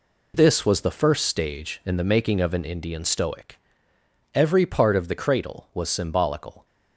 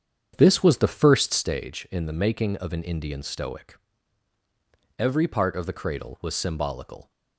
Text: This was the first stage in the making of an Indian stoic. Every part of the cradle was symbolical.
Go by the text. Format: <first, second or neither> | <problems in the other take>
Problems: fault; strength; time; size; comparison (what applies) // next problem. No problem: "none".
first | starts louder than the rest; strong; until 1.6 s; 8 dB